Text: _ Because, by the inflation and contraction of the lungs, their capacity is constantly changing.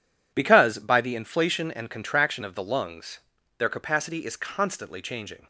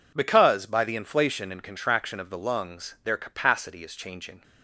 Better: first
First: none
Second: skips "constantly"; at 3.9 s

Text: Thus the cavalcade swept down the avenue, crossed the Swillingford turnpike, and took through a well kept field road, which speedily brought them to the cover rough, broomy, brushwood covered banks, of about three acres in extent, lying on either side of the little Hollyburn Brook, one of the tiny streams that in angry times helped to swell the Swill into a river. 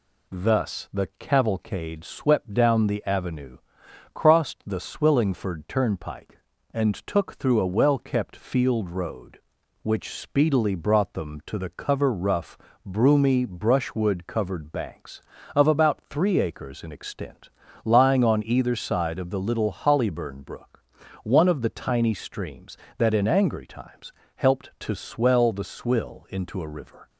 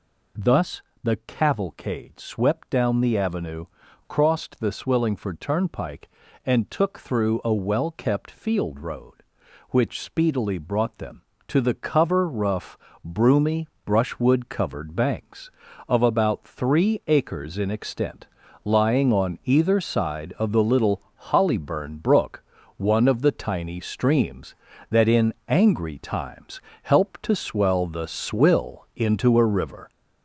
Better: first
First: pauses between "times" and "helped"; slight; at 24.1 s; 0.26 s long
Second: gets louder; noticeable; throughout; 5.5 dB // pauses between "Thus" and "the"; slight; at 0.8 s; 0.20 s long // pauses between "little" and "Hollyburn"; slight; at 21.0 s; 0.30 s long // pauses between "in" and "angry"; slight; at 25.3 s; 0.16 s long // pauses between "times" and "helped"; slight; at 26.6 s; 0.22 s long

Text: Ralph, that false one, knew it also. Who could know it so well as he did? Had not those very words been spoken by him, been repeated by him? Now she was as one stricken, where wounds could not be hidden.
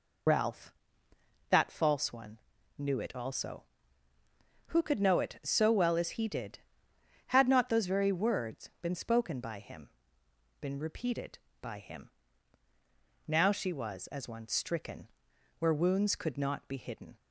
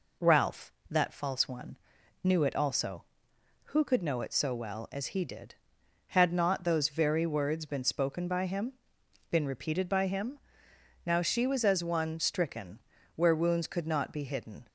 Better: second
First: loses the start of "Ralph"; at 0.2 s; 45 ms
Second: none

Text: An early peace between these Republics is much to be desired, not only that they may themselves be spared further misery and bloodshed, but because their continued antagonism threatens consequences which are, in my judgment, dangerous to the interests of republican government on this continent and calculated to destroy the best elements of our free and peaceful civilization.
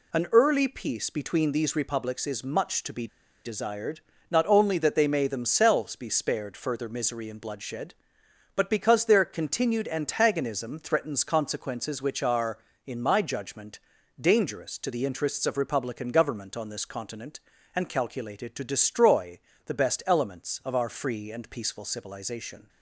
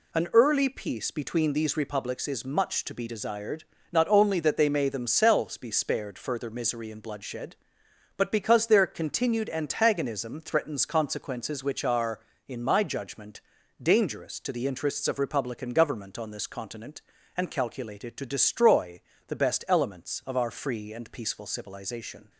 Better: second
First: pauses between "be" and "desired"; at 3.0 s; 0.38 s long // pauses between "destroy" and "the"; slight; at 19.3 s; 0.26 s long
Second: pauses between "destroy" and "the"; slight; at 18.9 s; 0.26 s long

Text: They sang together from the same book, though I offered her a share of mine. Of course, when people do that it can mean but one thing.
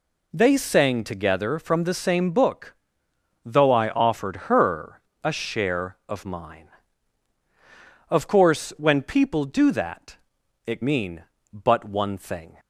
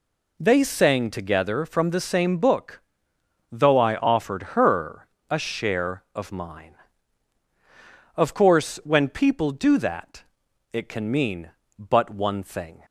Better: second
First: pauses between "her" and "a"; slight; at 5.0 s; 0.22 s long // pauses between "that" and "it"; noticeable; at 10.1 s; 0.48 s long // skips "can"; at 10.8 s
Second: pauses between "her" and "a"; slight; at 5.0 s; 0.22 s long // pauses between "that" and "it"; noticeable; at 10.2 s; 0.48 s long

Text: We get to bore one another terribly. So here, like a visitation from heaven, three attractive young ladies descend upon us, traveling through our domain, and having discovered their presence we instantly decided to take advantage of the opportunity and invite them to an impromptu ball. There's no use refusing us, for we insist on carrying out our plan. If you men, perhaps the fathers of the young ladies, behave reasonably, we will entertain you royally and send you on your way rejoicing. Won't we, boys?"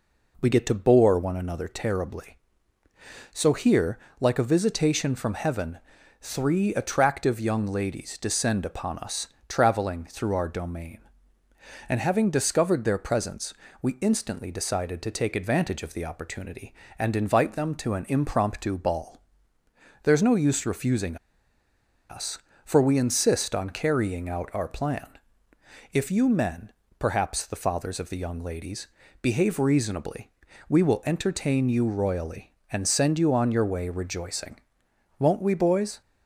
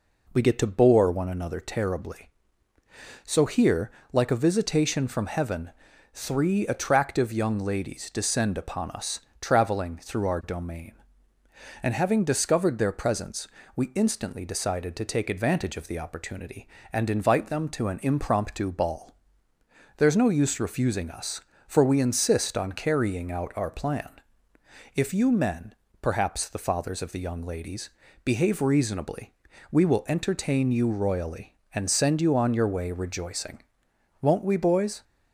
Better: second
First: pauses between "presence" and "we"; slight; at 13.5 s; 0.28 s long // pauses between "refusing" and "us"; noticeable; at 21.1 s; 0.94 s long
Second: pauses between "presence" and "we"; slight; at 13.4 s; 0.28 s long

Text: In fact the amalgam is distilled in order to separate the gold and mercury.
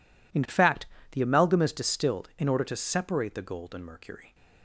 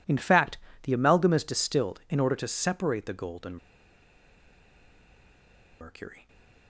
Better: first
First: pauses between "fact" and "the"; slight; at 0.8 s; 0.24 s long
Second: pauses between "fact" and "the"; slight; at 0.5 s; 0.24 s long // pauses between "and" and "mercury"; strong; at 3.5 s; 2.2 s long // stays silent after the last word; slight; from 6.1 s on; 0.5 s long

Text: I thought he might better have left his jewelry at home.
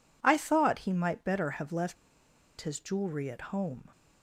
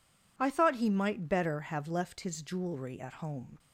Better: second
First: pauses between "left" and "his"; noticeable; at 1.9 s; 0.64 s long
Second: none

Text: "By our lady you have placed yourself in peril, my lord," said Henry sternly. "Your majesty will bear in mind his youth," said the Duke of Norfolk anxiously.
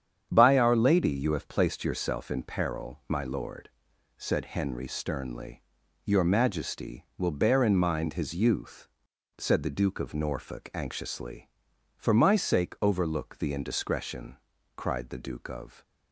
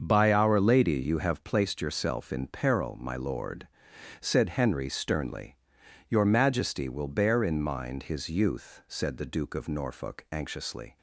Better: second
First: starts louder than the rest; strong; until 1.3 s; 8.5 dB // goes on to say "For my sake overlook the indiscretion cried the Duke of"; strong; from 11.9 s on; 3.8 s long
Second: starts louder than the rest; until 1.0 s; 6.5 dB

